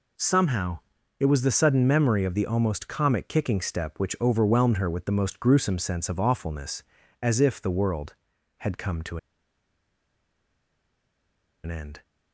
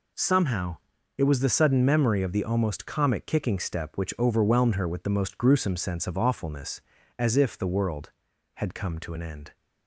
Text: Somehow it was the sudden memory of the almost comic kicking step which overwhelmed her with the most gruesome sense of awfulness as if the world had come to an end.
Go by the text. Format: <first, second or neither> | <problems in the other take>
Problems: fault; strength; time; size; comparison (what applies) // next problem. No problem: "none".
second | pauses between "Somehow" and "it"; at 0.7 s; 0.40 s long; also in the second // pauses between "to" and "an"; strong; at 9.1 s; 2.4 s long